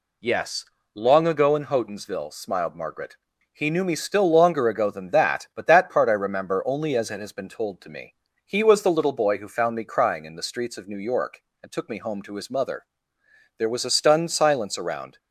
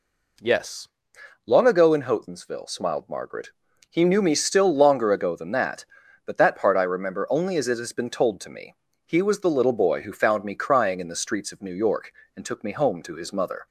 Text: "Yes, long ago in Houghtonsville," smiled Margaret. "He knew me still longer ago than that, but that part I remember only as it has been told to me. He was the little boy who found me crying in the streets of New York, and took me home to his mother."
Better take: second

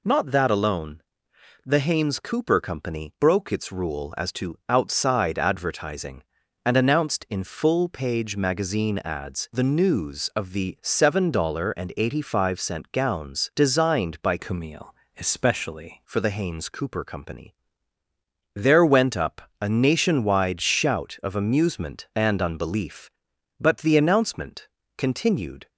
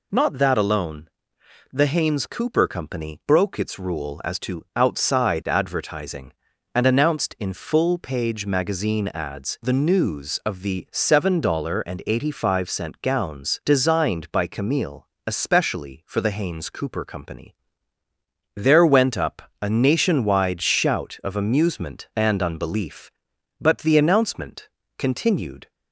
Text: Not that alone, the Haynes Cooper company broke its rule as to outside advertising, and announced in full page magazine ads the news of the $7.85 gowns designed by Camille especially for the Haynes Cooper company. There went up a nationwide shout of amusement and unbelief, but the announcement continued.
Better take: second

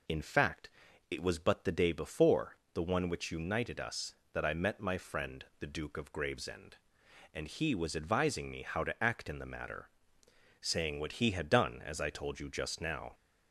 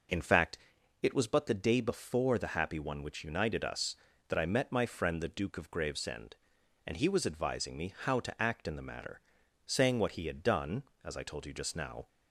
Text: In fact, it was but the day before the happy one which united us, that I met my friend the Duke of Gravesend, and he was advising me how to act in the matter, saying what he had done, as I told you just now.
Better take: second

